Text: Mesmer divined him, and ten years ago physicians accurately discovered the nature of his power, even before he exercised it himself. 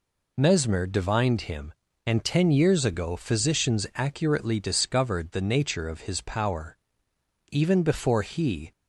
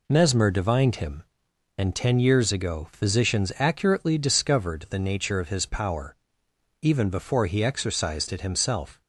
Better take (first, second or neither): second